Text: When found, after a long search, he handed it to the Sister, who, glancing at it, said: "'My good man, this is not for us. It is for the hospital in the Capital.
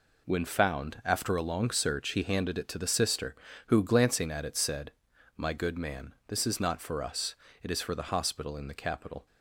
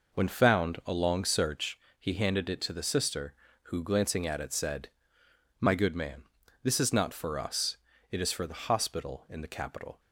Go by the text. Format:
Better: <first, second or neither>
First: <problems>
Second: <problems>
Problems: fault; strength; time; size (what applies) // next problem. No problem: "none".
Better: first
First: none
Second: skips "after"; at 0.8 s